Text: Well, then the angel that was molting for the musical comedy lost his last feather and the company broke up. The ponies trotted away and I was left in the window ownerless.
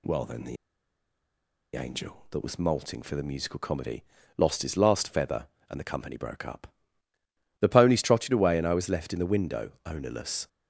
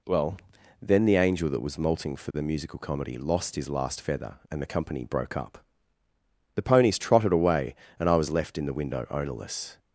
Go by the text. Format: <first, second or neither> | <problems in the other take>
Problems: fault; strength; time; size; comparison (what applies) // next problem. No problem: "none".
second | pauses between "the" and "angel"; at 0.5 s; 1.1 s long // pauses between "comedy" and "lost"; slight; at 4.0 s; 0.36 s long // pauses between "window" and "ownerless"; slight; at 9.6 s; 0.16 s long